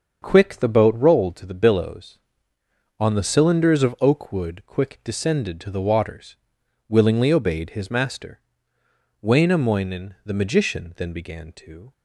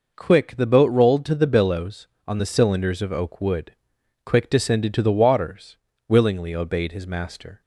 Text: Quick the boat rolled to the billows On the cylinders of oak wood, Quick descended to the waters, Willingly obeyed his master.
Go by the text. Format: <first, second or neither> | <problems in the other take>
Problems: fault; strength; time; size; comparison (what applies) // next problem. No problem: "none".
second | starts louder than the rest; until 1.2 s; 7 dB // goes on to say "Wainamoinen the magician Then began to"; strong; from 9.2 s on; 2.7 s long